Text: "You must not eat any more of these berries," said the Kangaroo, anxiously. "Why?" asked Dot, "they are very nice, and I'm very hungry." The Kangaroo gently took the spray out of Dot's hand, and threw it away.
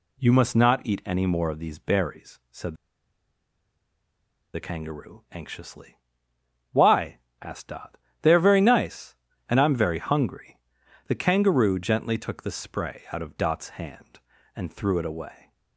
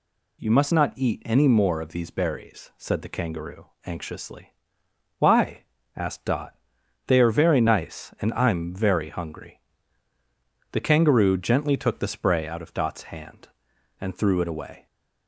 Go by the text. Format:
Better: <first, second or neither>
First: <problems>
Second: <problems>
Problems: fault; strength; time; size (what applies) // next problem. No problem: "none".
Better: second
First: pauses between "said" and "the"; strong; at 2.7 s; 1.7 s long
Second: none